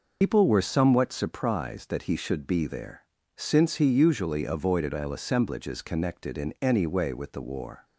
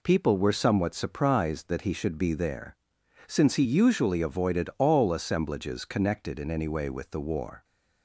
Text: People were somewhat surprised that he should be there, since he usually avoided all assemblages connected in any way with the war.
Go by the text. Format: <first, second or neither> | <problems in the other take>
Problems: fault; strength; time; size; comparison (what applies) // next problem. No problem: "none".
second | loses the start of "People"; at 0.2 s; 110 ms